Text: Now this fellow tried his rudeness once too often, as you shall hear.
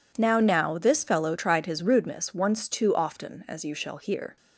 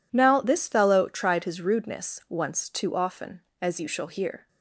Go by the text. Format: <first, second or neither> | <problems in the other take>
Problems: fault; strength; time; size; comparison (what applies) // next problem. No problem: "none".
second | says "Now" twice; at 0.4 s